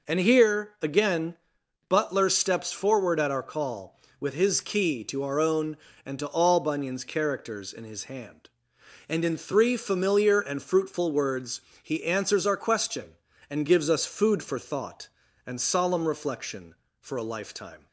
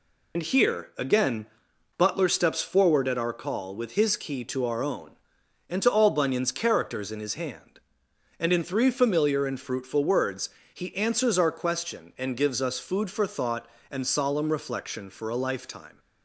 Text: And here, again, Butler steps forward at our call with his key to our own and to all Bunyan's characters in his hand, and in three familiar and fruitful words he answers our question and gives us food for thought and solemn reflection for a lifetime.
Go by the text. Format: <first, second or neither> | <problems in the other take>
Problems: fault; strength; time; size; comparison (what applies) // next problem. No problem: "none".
first | loses the start of "And"; at 0.3 s; 75 ms // pauses between "words" and "he"; slight; at 10.4 s; 0.24 s long; slight in the first